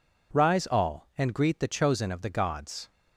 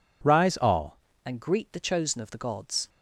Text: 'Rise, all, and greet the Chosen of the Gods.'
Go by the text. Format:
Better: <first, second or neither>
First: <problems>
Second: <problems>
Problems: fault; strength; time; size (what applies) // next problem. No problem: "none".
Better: first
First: none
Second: changes voice at "and"; from 1.2 s on; 1.6 s long